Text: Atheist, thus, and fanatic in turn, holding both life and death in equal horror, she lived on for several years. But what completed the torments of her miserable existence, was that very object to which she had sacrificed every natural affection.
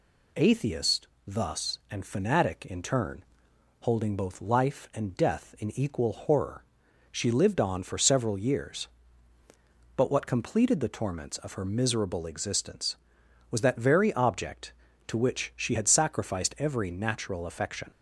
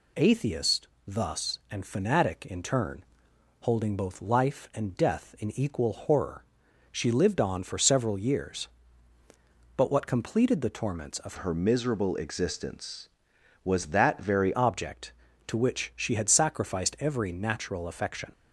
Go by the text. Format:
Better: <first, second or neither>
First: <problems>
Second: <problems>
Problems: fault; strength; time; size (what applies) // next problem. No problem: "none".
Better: first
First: none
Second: changes voice from "her" to "very"; from 11.3 to 14.5 s; 3.2 s long